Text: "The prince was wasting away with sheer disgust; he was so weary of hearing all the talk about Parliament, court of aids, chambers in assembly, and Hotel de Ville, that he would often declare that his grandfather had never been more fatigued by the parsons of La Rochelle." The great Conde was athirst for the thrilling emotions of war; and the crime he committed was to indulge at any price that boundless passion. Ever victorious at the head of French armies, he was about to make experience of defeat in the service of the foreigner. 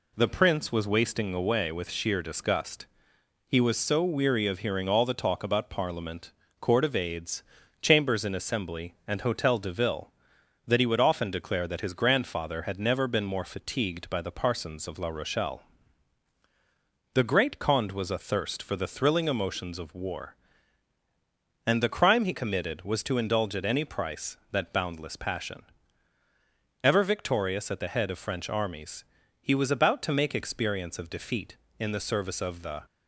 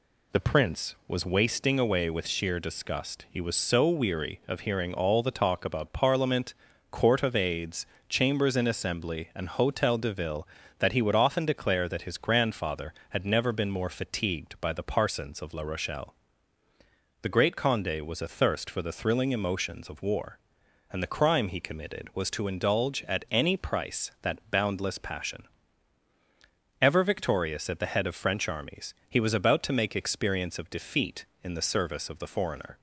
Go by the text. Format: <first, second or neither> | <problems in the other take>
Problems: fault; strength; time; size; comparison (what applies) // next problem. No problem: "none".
second | stops before "foreigner"; at 32.8 s